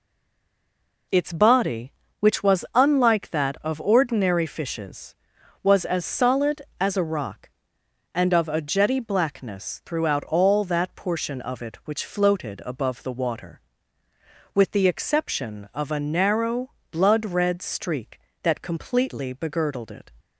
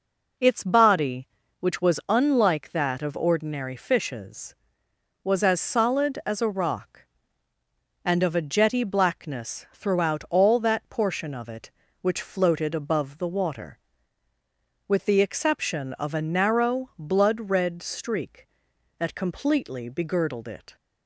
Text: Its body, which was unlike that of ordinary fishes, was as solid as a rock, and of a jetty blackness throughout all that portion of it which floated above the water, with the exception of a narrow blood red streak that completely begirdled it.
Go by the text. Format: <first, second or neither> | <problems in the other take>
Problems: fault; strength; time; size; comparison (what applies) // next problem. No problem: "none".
second | stays silent before the first word; until 1.0 s; 1.0 s long // pauses between "narrow" and "blood"; slight; at 16.6 s; 0.20 s long